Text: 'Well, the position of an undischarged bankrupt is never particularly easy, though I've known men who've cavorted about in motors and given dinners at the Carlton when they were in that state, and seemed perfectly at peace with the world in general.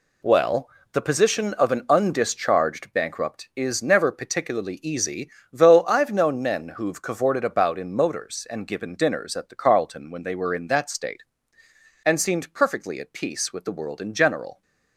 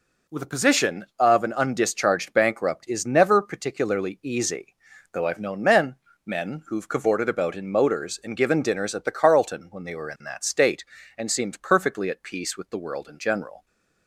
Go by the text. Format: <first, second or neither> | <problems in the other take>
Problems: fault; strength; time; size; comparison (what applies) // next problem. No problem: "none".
first | says "men" twice; at 6.2 s